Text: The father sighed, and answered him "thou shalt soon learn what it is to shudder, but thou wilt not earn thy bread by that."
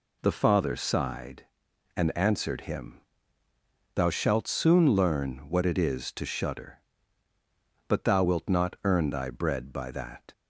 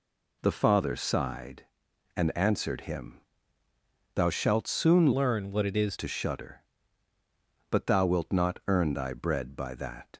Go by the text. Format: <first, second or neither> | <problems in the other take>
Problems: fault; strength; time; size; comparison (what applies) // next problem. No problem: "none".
first | pauses between "him" and "thou"; noticeable; at 3.1 s; 0.96 s long; noticeable in the first // changes voice from "learn" to "is"; from 5.1 to 5.9 s; 0.8 s long